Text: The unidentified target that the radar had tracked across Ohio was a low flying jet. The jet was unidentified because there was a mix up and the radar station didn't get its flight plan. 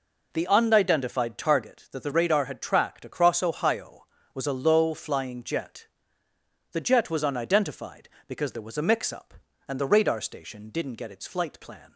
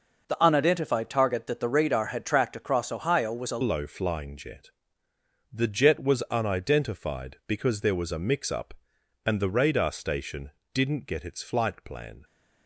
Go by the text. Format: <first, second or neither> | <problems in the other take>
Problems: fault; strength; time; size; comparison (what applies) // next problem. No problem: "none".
first | changes voice at "low"; from 3.6 s on; 8.6 s long // pauses between "station" and "didn't"; slight; at 10.5 s; 0.22 s long